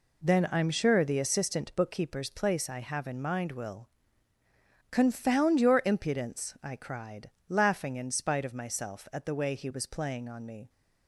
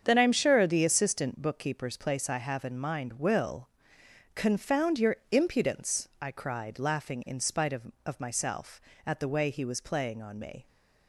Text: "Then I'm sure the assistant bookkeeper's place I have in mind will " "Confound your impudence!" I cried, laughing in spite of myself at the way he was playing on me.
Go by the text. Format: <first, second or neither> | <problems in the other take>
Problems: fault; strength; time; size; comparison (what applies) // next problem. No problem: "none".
first | starts louder than the rest; strong; until 1.0 s; 7.5 dB // pauses between "your" and "impudence"; slight; at 5.1 s; 0.16 s long // says "of" twice; at 8.0 s